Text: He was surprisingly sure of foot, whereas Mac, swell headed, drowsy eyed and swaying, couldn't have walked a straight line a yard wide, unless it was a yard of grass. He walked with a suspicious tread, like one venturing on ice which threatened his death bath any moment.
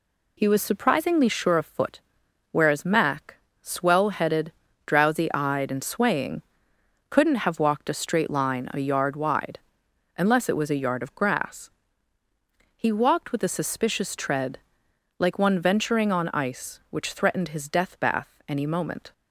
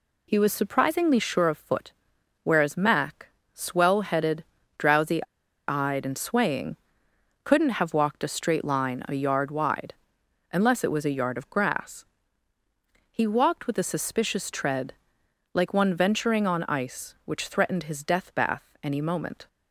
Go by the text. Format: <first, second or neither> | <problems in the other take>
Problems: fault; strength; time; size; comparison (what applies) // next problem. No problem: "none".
first | pauses between "drowsy" and "eyed"; at 5.2 s; 0.42 s long